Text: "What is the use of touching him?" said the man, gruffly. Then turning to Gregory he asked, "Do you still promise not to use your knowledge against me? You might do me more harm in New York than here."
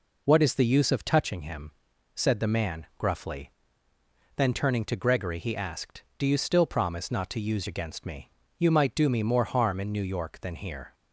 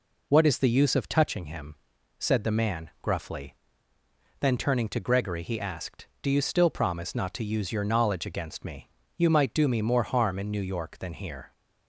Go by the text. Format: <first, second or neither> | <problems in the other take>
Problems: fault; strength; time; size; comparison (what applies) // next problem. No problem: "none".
second | skips "your knowledge"; at 7.6 s